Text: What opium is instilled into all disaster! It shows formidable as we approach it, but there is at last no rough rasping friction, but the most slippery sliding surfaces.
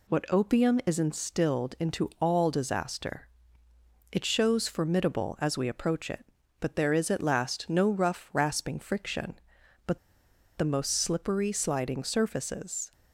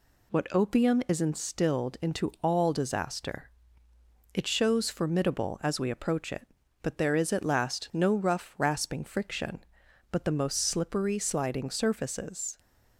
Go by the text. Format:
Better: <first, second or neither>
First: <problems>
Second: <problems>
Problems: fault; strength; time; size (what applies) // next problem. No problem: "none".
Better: second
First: pauses between "but" and "the"; noticeable; at 9.9 s; 0.58 s long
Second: none